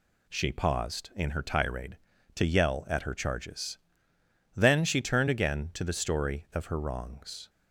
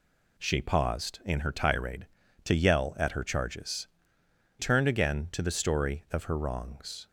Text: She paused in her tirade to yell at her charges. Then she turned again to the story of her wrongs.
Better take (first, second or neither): first